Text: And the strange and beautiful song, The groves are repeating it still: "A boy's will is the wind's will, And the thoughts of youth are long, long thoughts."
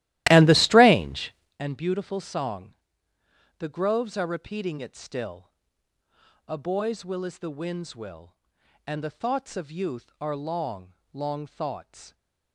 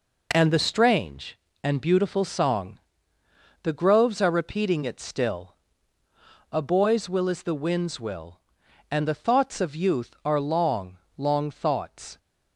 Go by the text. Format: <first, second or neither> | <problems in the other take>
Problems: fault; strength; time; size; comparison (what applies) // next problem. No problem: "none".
second | starts louder than the rest; strong; until 1.6 s; 15.5 dB